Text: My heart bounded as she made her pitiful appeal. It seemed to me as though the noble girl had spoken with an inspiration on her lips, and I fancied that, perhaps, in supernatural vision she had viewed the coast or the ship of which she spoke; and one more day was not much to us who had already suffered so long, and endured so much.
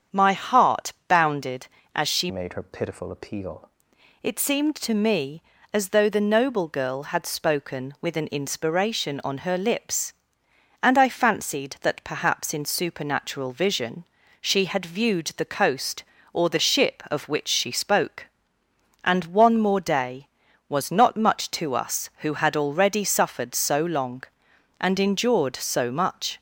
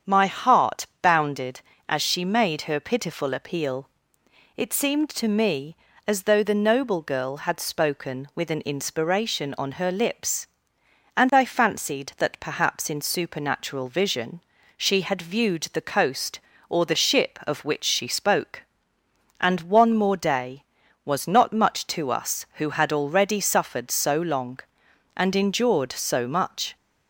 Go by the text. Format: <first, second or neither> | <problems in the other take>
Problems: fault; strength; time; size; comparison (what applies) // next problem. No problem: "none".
second | starts louder than the rest; strong; until 1.2 s; 8 dB; strong in the second // pauses between "heart" and "bounded"; slight; at 0.9 s; 0.16 s long; slight in the second // changes voice from "made" to "appeal"; from 2.2 to 3.6 s; 1.4 s long // pauses between "vision" and "she"; slight; at 14.0 s; 0.34 s long; slight in the second